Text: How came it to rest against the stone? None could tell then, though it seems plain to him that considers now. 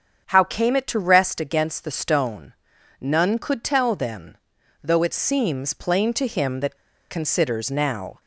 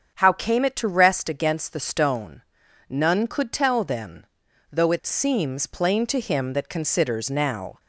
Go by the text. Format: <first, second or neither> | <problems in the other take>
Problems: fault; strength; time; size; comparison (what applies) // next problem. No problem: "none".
second | starts louder than the rest; strong; until 1.3 s; 7.5 dB; also in the second // pauses between "that" and "considers"; slight; at 6.7 s; 0.34 s long